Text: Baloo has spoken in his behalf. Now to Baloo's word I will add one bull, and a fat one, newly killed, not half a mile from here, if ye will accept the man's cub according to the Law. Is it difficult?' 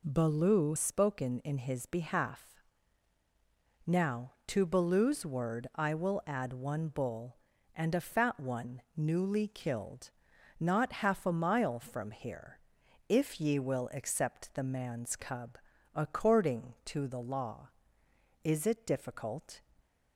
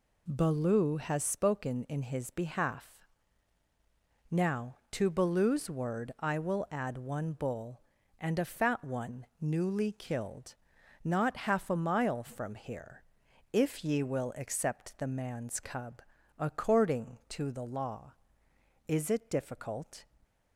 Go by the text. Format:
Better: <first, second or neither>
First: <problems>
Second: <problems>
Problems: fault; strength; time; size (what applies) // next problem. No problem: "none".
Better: second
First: skips "has"; at 0.7 s // pauses between "cub" and "according"; at 15.5 s; 0.38 s long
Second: pauses between "cub" and "according"; at 16.0 s; 0.38 s long